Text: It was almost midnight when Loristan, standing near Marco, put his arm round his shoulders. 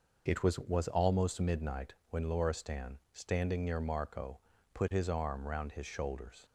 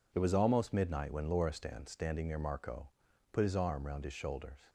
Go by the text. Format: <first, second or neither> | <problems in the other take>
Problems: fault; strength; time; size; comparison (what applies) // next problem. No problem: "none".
second | says "was" twice; at 0.5 s // pauses between "midnight" and "when"; slight; at 1.9 s; 0.16 s long